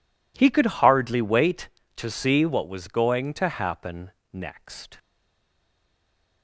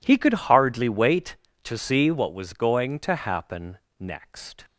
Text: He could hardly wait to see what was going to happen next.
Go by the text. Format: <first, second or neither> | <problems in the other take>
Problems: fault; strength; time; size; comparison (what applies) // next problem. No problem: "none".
second | pauses between "happen" and "next"; slight; at 4.1 s; 0.22 s long; slight in the second // stays silent after the last word; noticeable; from 4.9 s on; 1.5 s long